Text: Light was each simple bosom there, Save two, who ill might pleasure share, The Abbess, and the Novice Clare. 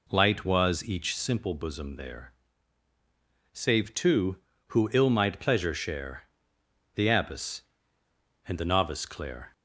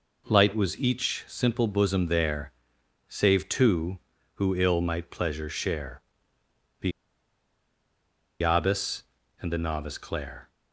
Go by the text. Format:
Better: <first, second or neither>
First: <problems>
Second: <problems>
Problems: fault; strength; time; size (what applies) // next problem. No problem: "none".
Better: first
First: none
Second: pauses between "The" and "Abbess"; strong; at 6.9 s; 1.5 s long